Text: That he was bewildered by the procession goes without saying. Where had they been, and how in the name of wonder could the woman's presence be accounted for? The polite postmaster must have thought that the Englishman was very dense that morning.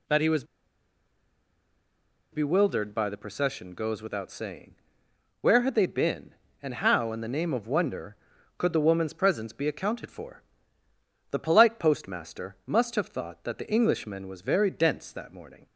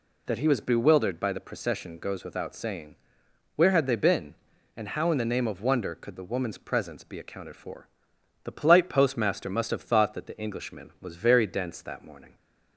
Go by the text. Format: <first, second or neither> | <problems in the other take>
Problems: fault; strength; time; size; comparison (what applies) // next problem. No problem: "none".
second | pauses between "was" and "bewildered"; strong; at 0.4 s; 1.8 s long